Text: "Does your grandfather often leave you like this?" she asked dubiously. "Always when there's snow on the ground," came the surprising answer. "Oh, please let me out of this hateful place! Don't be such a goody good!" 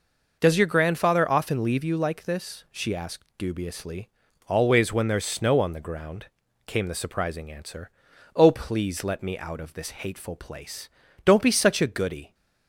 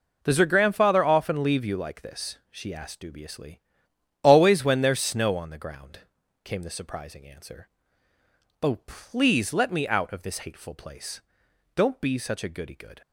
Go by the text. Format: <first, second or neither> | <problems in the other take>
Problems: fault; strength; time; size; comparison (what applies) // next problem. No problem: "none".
second | stops before "good"; at 12.3 s